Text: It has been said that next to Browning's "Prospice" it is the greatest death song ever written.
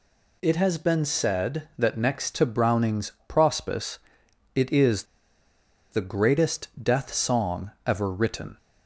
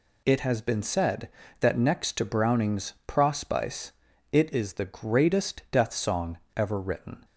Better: second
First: pauses between "Prospice" and "it"; noticeable; at 3.9 s; 0.56 s long // pauses between "is" and "the"; noticeable; at 5.0 s; 0.87 s long // pauses between "song" and "ever"; slight; at 7.6 s; 0.16 s long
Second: pauses between "Prospice" and "it"; at 3.9 s; 0.40 s long // pauses between "song" and "ever"; slight; at 6.3 s; 0.17 s long

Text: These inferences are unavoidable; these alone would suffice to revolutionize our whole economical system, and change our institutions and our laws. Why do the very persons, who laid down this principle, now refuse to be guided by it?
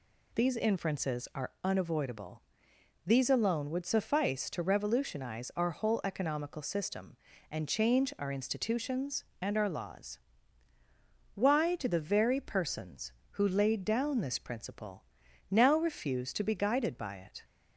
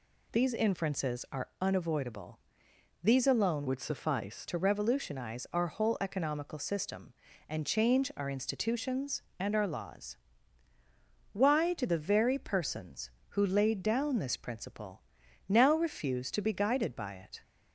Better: first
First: none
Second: changes voice from "would" to "suffice"; from 3.6 to 4.4 s; 0.8 s long

